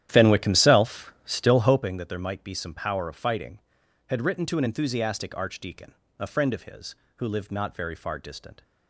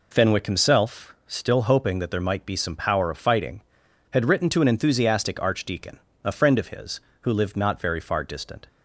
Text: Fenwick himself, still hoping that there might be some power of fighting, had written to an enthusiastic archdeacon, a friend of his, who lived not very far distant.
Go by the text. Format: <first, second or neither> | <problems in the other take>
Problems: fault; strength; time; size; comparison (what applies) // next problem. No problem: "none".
second | starts louder than the rest; strong; until 1.9 s; 11 dB